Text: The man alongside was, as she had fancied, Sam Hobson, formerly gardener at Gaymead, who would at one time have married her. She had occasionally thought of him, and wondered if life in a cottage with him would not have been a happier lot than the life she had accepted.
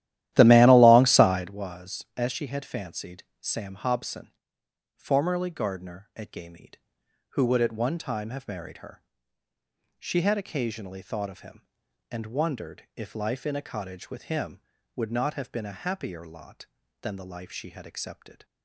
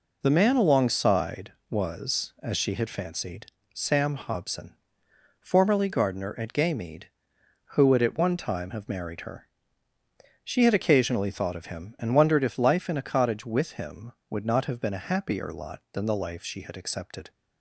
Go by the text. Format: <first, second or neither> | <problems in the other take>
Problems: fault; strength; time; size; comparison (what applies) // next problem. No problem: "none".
second | starts louder than the rest; strong; until 1.6 s; 13.5 dB